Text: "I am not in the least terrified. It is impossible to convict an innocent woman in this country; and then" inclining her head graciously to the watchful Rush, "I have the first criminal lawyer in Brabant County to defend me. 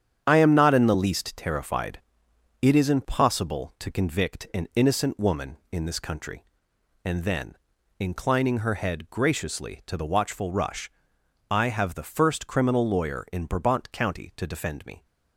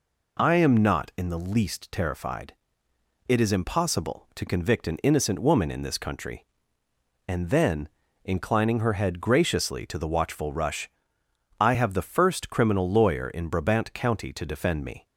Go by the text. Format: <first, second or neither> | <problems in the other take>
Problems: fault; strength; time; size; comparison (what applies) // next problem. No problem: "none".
second | gets quieter; strong; throughout; 7.5 dB // pauses between "then" and "inclining"; at 7.5 s; 0.42 s long; slight in the second